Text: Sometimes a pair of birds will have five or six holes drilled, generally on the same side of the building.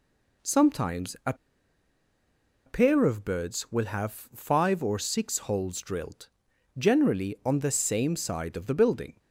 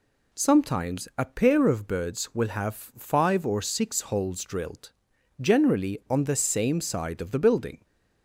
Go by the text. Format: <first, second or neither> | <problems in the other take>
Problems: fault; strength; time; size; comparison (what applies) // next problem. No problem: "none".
second | pauses between "a" and "pair"; strong; at 1.3 s; 1.3 s long